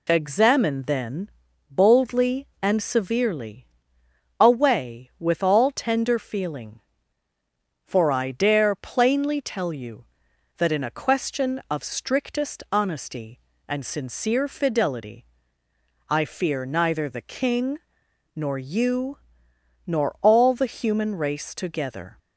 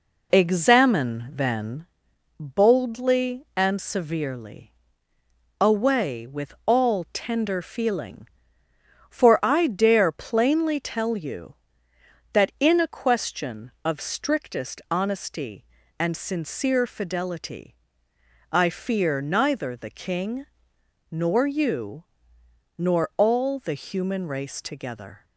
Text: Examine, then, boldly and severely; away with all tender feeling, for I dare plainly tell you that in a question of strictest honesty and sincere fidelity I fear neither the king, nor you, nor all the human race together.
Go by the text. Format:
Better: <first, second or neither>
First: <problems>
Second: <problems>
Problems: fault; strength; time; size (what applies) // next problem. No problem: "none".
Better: first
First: pauses between "fidelity" and "I"; noticeable; at 15.2 s; 0.82 s long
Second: starts louder than the rest; until 1.8 s; 4 dB // pauses between "fidelity" and "I"; noticeable; at 17.7 s; 0.78 s long